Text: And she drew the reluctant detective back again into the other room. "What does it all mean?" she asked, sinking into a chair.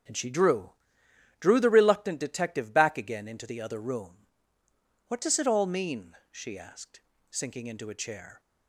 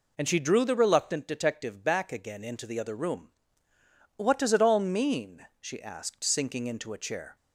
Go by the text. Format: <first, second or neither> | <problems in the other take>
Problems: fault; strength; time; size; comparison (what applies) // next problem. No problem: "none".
second | starts louder than the rest; strong; until 1.7 s; 8 dB // says "drew" twice; at 1.4 s